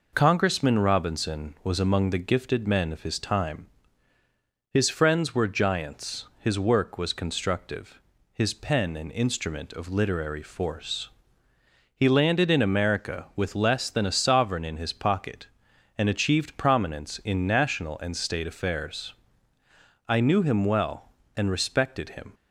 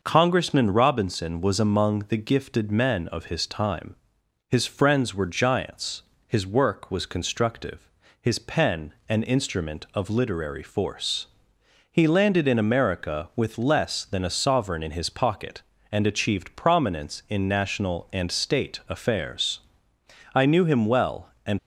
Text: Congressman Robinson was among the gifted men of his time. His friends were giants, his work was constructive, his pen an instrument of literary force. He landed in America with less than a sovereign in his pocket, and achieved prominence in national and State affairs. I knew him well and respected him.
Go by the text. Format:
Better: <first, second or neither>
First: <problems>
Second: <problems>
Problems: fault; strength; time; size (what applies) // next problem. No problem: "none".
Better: first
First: none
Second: pauses between "pen" and "an"; slight; at 8.9 s; 0.16 s long // stops before "respected him"; at 21.5 s